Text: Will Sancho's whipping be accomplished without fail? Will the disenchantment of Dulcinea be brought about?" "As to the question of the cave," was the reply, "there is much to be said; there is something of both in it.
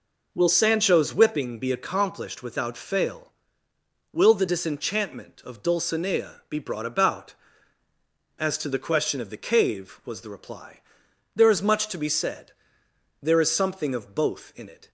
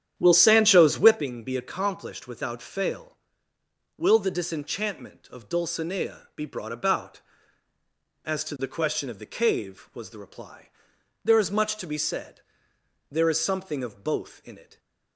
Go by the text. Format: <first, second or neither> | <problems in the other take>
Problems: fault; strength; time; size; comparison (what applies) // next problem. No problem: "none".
first | starts louder than the rest; strong; until 1.2 s; 9.5 dB